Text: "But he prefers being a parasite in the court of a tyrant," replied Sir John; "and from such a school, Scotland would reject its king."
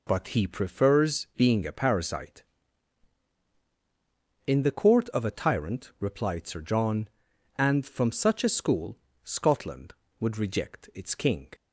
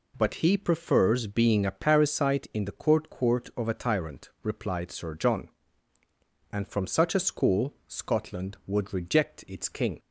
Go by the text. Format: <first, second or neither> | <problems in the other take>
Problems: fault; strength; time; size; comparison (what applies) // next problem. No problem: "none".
first | says "court" twice; at 3.0 s